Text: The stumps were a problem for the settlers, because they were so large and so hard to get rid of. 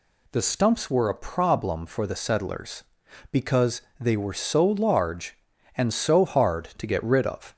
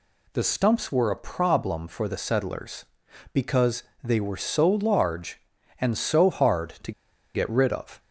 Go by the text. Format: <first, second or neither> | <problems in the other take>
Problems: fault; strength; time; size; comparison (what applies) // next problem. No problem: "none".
first | pauses between "because" and "they"; slight; at 3.8 s; 0.22 s long; slight in the first // pauses between "to" and "get"; at 6.9 s; 0.42 s long